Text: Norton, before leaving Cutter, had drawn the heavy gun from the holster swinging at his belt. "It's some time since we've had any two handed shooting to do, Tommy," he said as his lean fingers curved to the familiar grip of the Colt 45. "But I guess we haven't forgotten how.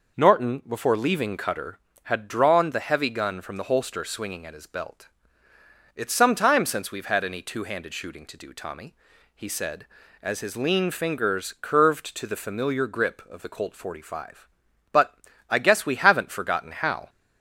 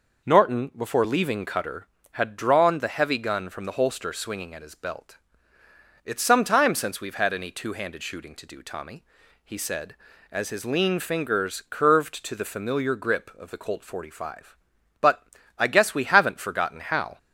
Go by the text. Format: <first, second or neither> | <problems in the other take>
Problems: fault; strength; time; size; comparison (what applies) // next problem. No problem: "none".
neither | pauses between "But" and "I"; slight; the same in both